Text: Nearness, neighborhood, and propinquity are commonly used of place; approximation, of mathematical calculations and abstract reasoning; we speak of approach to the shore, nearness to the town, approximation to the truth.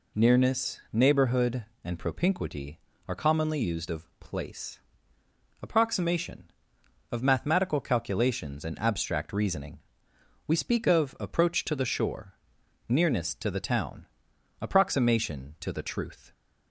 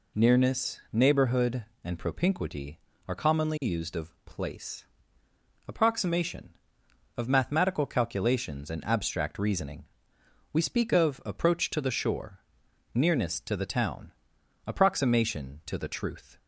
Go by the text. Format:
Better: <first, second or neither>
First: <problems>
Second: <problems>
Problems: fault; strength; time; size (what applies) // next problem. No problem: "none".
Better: neither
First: none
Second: none